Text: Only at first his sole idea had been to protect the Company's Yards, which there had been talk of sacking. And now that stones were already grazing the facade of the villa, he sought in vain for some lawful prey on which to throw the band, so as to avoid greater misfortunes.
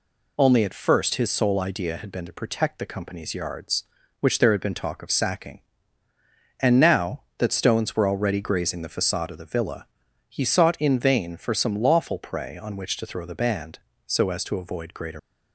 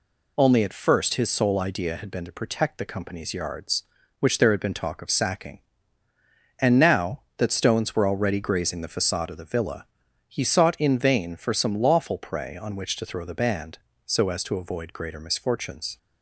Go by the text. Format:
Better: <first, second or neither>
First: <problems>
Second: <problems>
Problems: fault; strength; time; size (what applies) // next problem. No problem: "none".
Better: second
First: stops before "misfortunes"; at 15.1 s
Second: none